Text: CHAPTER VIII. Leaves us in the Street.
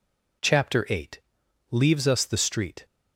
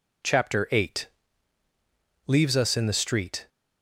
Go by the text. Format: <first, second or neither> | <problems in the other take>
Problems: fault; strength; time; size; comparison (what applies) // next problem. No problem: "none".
second | skips "in"; at 2.2 s